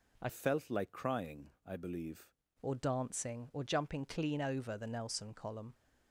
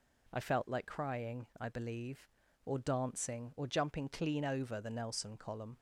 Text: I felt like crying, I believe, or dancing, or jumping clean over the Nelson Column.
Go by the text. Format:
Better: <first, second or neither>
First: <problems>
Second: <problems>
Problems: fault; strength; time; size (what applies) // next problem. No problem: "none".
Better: second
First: changes voice from "felt" to "believe"; from 0.2 to 2.3 s; 2.1 s long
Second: none